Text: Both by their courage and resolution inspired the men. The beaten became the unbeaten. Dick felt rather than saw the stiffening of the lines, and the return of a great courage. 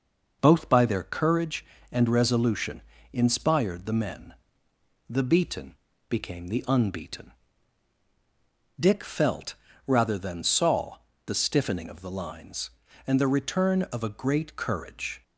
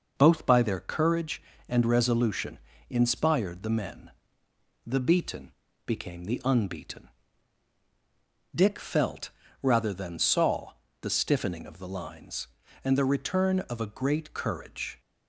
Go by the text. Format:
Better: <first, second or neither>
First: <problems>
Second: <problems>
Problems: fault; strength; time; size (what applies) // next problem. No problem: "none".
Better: neither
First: pauses between "resolution" and "inspired"; slight; at 2.8 s; 0.32 s long // pauses between "beaten" and "became"; slight; at 5.7 s; 0.34 s long // pauses between "felt" and "rather"; slight; at 9.5 s; 0.32 s long // pauses between "saw" and "the"; slight; at 10.9 s; 0.30 s long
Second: pauses between "resolution" and "inspired"; slight; at 2.5 s; 0.32 s long // pauses between "beaten" and "became"; slight; at 5.5 s; 0.34 s long // pauses between "felt" and "rather"; slight; at 9.2 s; 0.32 s long // pauses between "saw" and "the"; slight; at 10.7 s; 0.30 s long